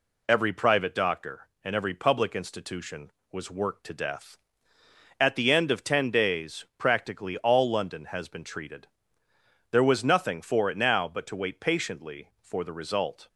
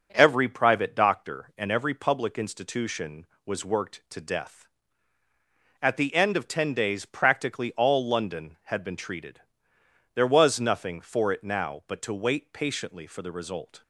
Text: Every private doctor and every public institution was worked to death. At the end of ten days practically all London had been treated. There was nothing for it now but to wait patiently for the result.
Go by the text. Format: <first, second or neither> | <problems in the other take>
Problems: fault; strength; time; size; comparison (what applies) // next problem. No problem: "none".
second | says "has" for "had"; at 8.0 s